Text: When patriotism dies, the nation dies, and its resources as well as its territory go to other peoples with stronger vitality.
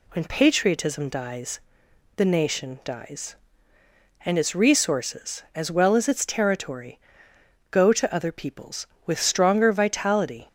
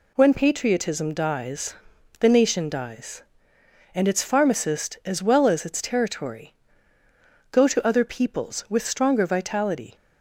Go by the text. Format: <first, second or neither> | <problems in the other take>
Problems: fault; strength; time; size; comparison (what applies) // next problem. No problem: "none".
first | says "pharmacist" for "resources"; at 4.2 s // pauses between "territory" and "go"; noticeable; at 6.5 s; 0.98 s long; noticeable in the first